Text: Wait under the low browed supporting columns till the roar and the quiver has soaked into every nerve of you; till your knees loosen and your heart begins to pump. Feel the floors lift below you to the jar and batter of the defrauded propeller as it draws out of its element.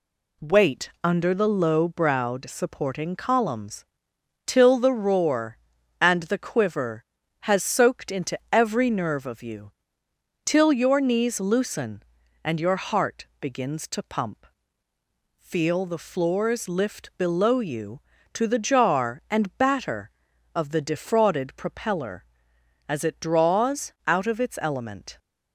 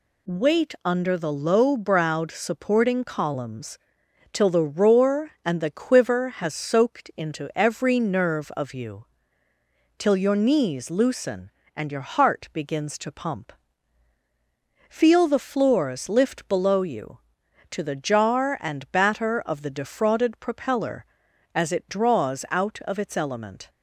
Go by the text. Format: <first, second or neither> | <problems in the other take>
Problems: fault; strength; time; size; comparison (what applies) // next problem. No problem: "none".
neither | pauses between "columns" and "till"; noticeable; the same in both